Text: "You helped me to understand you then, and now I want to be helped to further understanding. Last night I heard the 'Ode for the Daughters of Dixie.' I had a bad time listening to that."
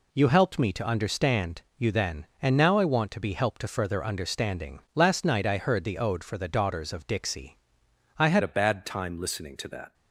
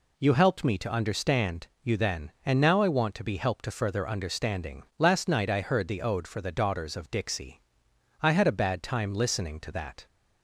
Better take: second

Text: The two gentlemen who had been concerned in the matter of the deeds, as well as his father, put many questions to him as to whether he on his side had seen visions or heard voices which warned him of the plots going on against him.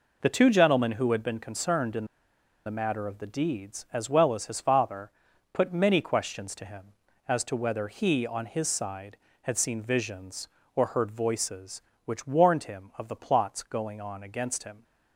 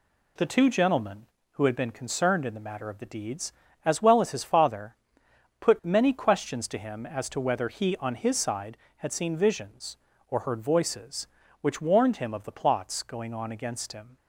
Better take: second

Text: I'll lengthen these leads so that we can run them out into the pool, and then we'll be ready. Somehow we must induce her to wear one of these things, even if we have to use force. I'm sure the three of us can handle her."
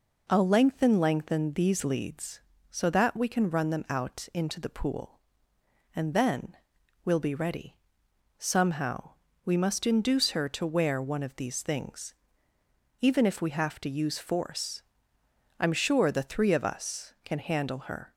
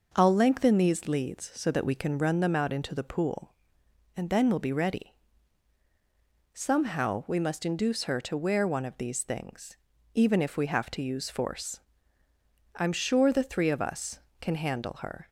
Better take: second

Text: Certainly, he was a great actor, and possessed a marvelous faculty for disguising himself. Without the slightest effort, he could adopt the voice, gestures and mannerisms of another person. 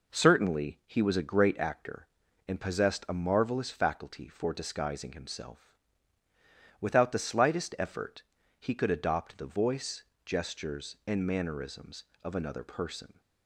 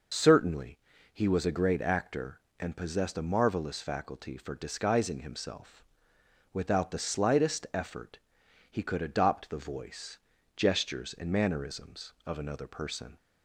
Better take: first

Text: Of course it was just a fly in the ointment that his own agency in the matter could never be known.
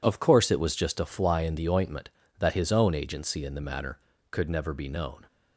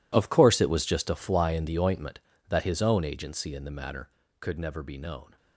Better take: first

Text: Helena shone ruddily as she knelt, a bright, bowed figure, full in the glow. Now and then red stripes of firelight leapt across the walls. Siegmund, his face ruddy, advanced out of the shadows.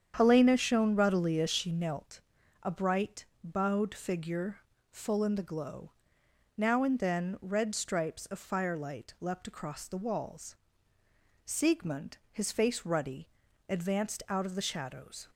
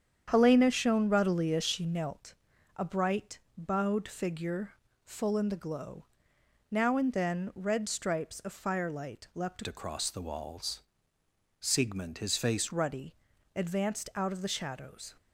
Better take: first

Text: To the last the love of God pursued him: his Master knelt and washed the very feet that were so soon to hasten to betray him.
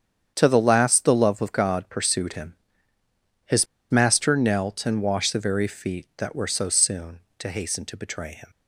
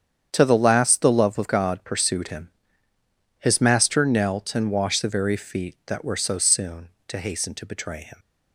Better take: second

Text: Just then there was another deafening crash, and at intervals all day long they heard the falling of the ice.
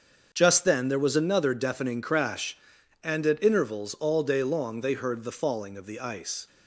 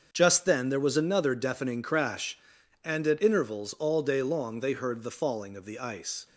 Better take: neither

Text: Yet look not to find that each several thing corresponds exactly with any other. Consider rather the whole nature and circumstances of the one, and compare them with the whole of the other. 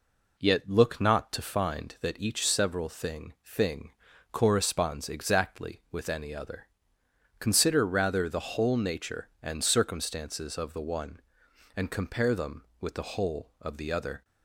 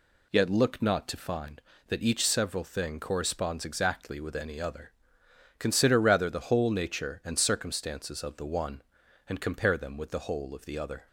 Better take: second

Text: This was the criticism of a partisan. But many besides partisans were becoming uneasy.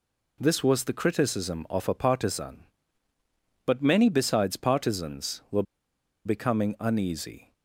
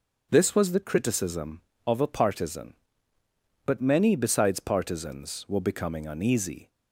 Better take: second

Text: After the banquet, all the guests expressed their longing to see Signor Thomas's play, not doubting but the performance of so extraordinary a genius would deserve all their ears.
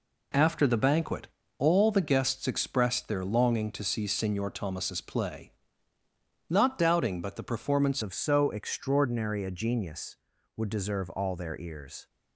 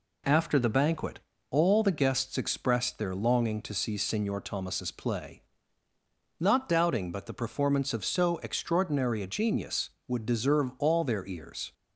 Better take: second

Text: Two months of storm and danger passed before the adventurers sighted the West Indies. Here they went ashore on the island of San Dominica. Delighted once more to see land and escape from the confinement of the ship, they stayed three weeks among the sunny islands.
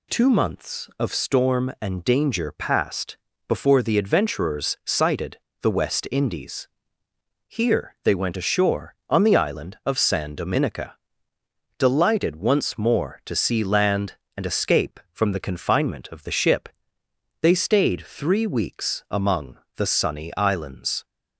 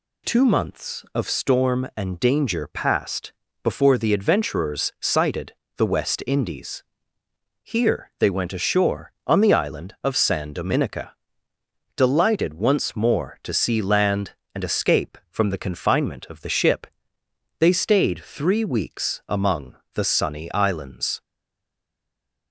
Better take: first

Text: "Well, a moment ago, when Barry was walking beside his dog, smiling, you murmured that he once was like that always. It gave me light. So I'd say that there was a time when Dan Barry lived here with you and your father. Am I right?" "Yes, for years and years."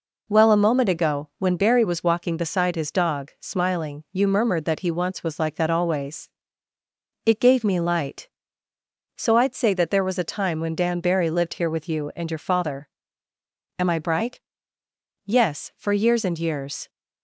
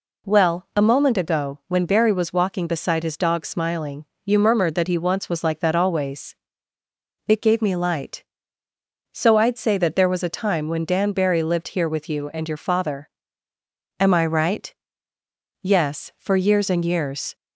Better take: second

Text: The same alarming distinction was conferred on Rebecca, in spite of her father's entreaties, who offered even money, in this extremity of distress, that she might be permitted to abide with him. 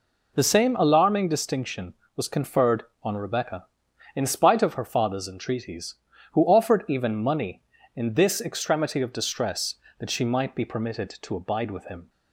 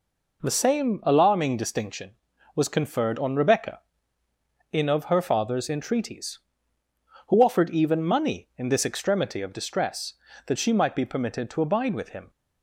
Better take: first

